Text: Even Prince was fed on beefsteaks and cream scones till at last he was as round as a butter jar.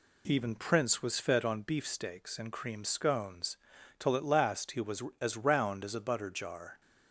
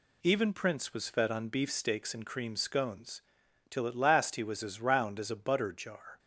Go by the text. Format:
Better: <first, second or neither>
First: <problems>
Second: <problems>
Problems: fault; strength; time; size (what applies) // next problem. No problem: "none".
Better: neither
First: pauses between "scones" and "till"; at 3.5 s; 0.44 s long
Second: pauses between "scones" and "till"; noticeable; at 3.2 s; 0.48 s long